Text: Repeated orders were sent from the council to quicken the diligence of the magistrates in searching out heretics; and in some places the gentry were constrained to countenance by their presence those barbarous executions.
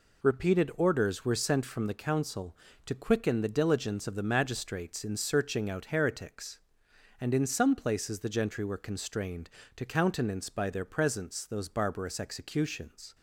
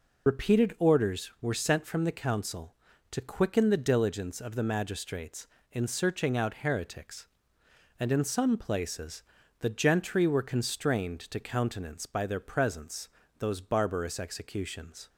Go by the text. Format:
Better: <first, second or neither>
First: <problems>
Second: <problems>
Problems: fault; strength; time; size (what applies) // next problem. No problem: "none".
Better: first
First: none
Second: loses the start of "Repeated"; at 0.2 s; 65 ms // pauses between "places" and "the"; at 9.2 s; 0.38 s long // pauses between "presence" and "those"; slight; at 13.0 s; 0.32 s long